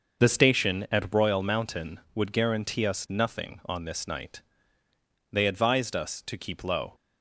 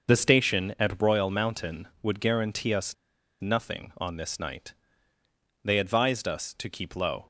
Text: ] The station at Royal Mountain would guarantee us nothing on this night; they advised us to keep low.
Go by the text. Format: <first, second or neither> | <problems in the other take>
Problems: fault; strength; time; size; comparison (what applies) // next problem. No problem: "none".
first | starts louder than the rest; noticeable; until 1.1 s; 6 dB; noticeable in the first // pauses between "us" and "nothing"; noticeable; at 2.9 s; 0.47 s long